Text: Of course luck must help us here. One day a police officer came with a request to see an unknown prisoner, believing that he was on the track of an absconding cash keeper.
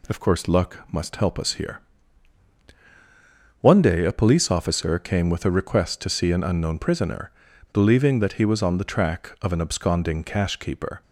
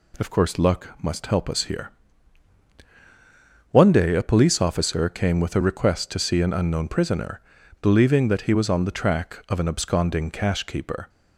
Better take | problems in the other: neither | none

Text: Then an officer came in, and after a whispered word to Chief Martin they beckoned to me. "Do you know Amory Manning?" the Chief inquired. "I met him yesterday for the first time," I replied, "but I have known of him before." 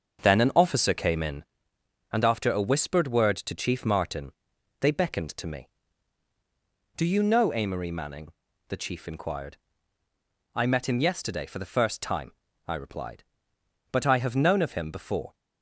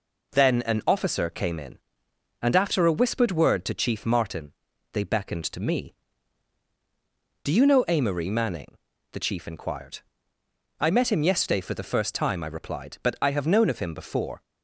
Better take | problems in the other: second | starts louder than the rest; until 1.5 s; 6.5 dB // pauses between "Martin" and "they"; noticeable; at 4.3 s; 0.48 s long; also in the second

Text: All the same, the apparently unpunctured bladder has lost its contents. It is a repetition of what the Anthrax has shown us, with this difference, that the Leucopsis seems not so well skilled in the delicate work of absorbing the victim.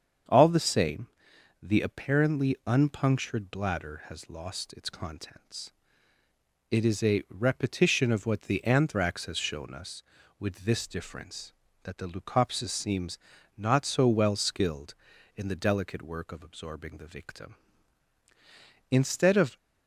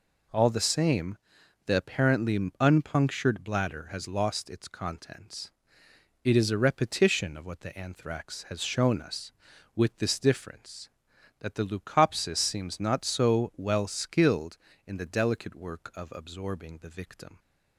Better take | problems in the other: second | starts louder than the rest; strong; until 1.8 s; 7.5 dB // pauses between "seems" and "not"; at 13.1 s; 0.38 s long // goes on to say "Instead of"; noticeable; from 18.8 s on; 0.66 s long

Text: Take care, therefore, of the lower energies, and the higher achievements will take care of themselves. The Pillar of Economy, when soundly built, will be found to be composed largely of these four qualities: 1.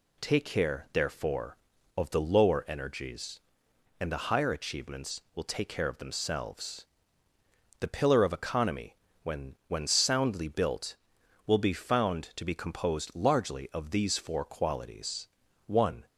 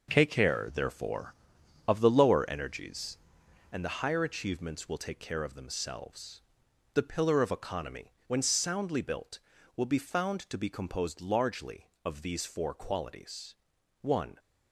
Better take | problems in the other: second | says "when" twice; at 9.6 s

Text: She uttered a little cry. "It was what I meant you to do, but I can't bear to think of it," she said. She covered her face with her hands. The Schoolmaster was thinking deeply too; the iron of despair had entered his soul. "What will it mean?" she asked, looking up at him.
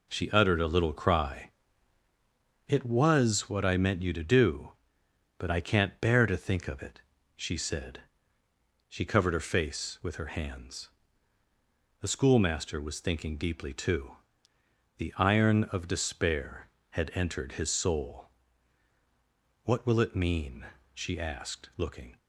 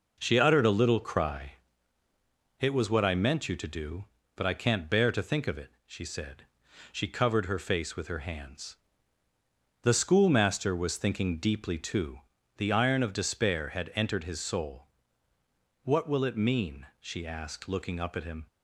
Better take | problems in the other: second | stops before "up at him"; at 22.1 s

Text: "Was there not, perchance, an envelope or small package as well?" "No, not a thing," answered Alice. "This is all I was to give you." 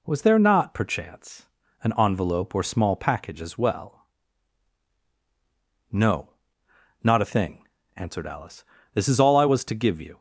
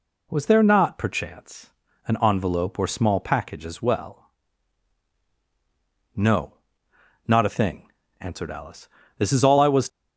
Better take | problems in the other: first | stops before "to give you"; at 9.8 s

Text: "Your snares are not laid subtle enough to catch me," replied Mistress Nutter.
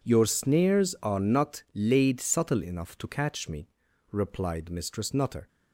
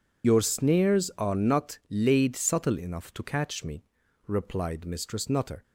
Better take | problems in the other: first | loses the start of "Your"; at 0.2 s; 60 ms

